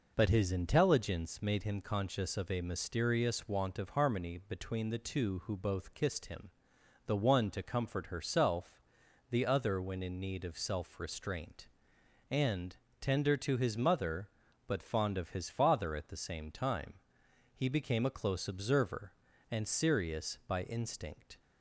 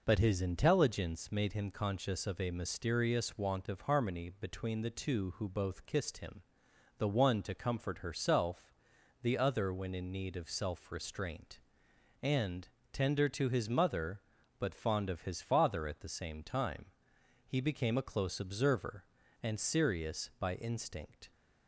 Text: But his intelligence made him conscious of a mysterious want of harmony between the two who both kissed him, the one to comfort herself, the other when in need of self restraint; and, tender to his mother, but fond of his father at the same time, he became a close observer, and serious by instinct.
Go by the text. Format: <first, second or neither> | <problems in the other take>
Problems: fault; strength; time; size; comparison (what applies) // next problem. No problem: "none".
neither | none